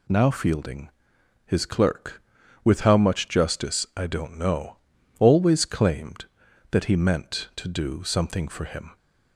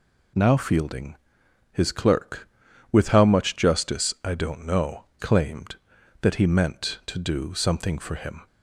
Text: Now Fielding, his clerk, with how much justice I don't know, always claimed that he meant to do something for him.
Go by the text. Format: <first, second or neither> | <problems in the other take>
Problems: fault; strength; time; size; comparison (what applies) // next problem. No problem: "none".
first | skips "always"; at 5.1 s